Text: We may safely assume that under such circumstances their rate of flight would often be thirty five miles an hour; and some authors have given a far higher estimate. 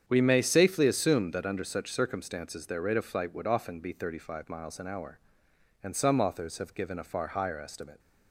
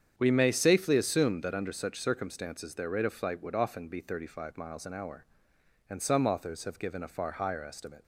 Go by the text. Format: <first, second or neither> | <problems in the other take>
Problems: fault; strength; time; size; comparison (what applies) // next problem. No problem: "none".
neither | starts louder than the rest; strong; the same in both